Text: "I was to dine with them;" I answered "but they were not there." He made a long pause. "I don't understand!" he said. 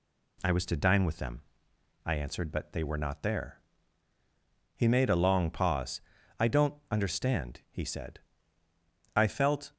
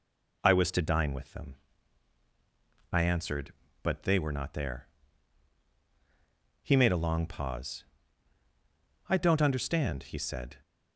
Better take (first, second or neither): second